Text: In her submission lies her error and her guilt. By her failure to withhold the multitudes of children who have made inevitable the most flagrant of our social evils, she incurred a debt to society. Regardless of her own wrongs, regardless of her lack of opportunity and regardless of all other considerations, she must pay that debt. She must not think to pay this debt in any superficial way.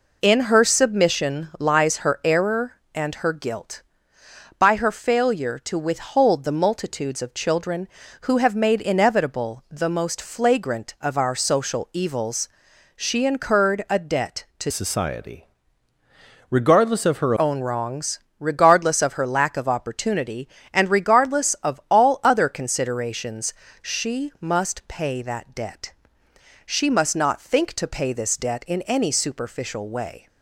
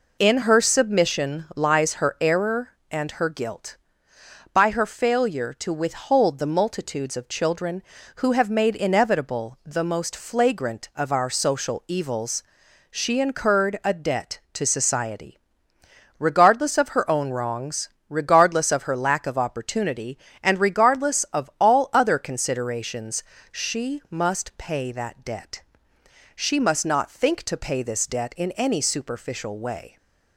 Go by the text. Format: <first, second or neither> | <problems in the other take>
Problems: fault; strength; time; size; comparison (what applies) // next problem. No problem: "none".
second | changes voice from "society" to "her"; from 14.7 to 17.3 s; 2.6 s long